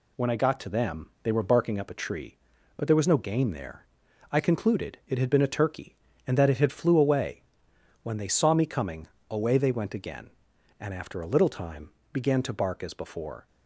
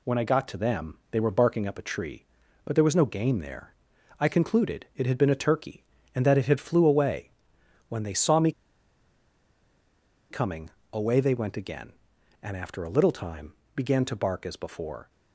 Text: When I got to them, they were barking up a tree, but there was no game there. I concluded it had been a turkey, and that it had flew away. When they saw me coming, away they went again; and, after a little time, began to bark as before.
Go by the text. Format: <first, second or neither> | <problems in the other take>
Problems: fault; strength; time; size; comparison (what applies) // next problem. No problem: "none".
first | pauses between "me" and "coming"; strong; at 8.5 s; 1.7 s long